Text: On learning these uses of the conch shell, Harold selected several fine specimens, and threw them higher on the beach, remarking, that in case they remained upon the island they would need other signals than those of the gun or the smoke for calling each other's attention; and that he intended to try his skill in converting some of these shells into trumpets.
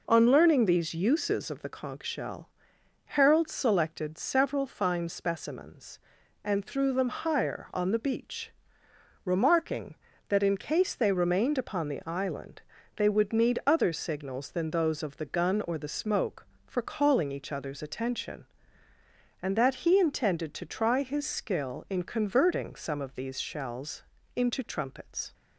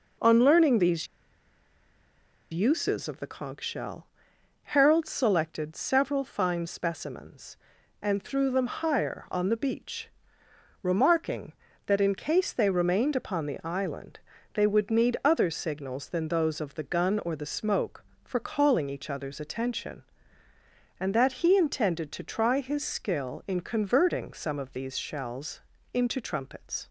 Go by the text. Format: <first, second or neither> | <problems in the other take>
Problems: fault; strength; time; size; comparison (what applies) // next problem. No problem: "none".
first | pauses between "these" and "uses"; strong; at 1.0 s; 1.4 s long // pauses between "island" and "they"; slight; at 14.1 s; 0.36 s long; slight in the first // pauses between "shells" and "into"; slight; at 25.6 s; 0.32 s long; slight in the first